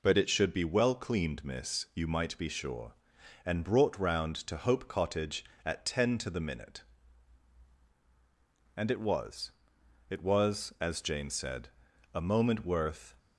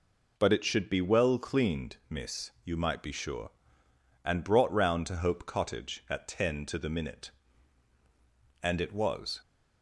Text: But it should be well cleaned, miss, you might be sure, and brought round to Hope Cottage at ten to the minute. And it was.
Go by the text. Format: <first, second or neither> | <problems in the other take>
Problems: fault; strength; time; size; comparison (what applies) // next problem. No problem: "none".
second | goes on to say "It was as Jane said a moment worth"; strong; from 10.0 s on; 3.0 s long